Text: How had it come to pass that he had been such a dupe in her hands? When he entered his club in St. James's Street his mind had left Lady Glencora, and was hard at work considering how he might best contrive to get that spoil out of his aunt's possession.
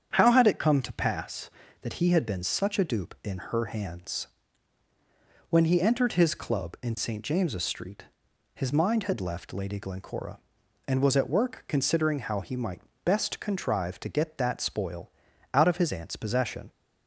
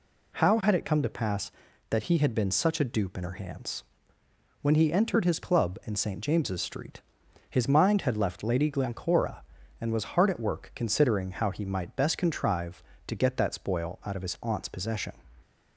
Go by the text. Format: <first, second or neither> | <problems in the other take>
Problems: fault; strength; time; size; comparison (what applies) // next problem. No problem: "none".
second | starts louder than the rest; strong; until 1.1 s; 8 dB // pauses between "Street" and "his"; noticeable; at 8.0 s; 0.50 s long; noticeable in the second // skips "hard"; at 11.1 s // pauses between "might" and "best"; slight; at 12.7 s; 0.24 s long // pauses between "spoil" and "out"; at 15.0 s; 0.42 s long